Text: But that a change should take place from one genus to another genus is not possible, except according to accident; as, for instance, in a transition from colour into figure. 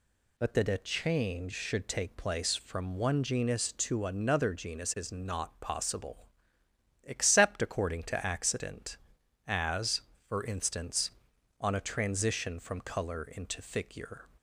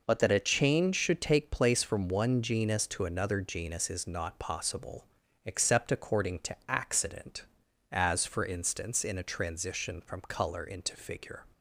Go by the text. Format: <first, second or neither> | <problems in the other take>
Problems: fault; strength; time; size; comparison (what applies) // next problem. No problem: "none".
second | says "on" for "in"; at 11.5 s